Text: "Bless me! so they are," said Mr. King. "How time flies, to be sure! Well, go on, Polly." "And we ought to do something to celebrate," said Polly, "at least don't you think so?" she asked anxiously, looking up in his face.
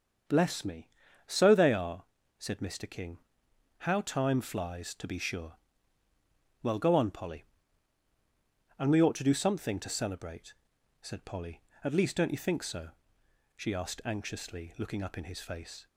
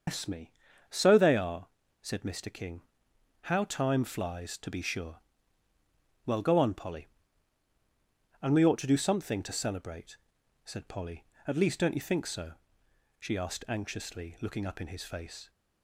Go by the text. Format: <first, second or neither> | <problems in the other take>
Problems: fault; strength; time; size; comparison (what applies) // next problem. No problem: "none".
first | loses the start of "Bless"; at 0.0 s; 155 ms // starts louder than the rest; until 1.4 s; 6.5 dB; also in the first